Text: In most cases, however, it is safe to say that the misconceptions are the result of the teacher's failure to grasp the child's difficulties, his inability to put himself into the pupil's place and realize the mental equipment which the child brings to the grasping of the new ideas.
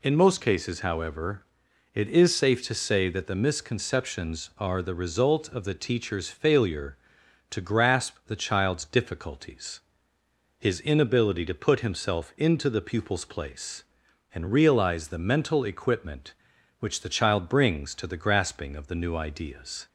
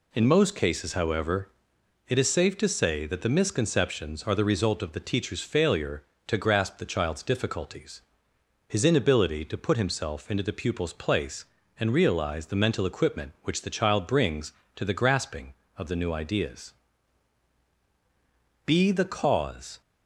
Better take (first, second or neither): first